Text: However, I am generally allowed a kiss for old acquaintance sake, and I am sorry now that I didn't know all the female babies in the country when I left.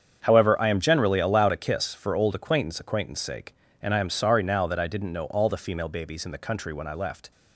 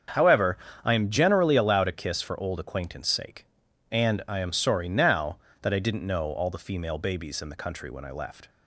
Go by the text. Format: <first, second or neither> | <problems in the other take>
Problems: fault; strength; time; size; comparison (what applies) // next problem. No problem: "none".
second | starts louder than the rest; strong; until 1.2 s; 7.5 dB; strong in the second // says "acquaintance" twice; at 2.7 s